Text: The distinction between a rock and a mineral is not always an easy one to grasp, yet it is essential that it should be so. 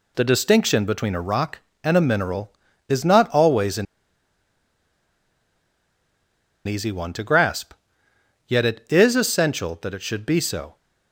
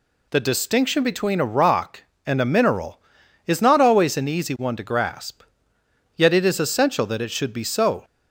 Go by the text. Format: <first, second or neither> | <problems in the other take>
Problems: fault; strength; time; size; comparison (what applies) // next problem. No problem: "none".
second | pauses between "an" and "easy"; strong; at 3.8 s; 2.8 s long